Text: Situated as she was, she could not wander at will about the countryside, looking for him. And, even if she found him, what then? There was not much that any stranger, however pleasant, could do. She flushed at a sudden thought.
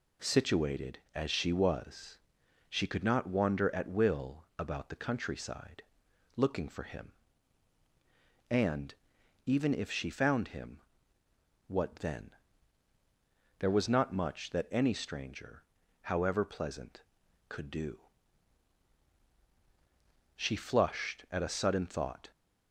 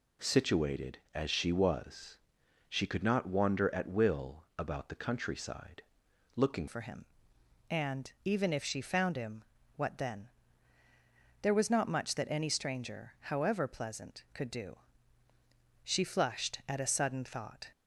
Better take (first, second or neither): first